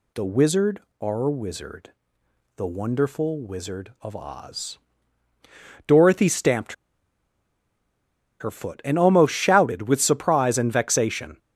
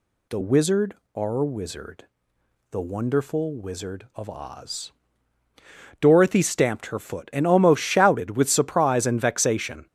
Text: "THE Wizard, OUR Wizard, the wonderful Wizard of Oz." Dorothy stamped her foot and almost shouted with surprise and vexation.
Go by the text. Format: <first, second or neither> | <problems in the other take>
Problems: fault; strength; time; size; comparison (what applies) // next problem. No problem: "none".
second | pauses between "stamped" and "her"; strong; at 6.7 s; 1.6 s long